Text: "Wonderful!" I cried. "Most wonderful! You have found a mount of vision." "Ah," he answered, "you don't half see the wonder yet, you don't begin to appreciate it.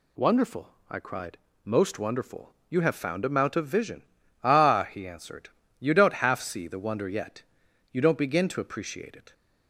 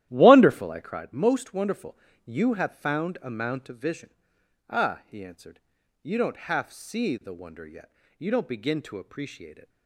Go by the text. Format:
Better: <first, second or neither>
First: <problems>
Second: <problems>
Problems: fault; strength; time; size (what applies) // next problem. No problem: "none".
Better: first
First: none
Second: starts louder than the rest; strong; until 1.1 s; 13 dB